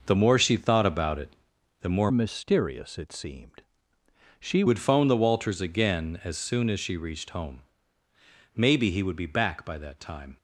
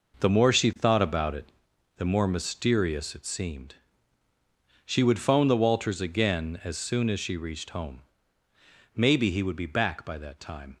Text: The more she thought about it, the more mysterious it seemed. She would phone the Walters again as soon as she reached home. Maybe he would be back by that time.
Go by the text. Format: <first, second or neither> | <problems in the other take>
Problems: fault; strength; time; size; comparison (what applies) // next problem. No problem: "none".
second | changes voice from "mysterious" to "She"; from 2.1 to 4.6 s; 2.5 s long